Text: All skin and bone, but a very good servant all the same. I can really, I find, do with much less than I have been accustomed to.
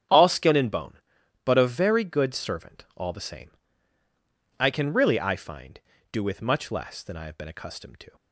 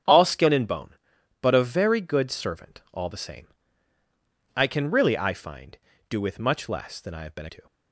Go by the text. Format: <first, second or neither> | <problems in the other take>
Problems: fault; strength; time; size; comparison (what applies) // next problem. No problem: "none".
first | starts louder than the rest; strong; until 1.5 s; 8.5 dB; strong in the first // skips "accustomed"; at 7.4 s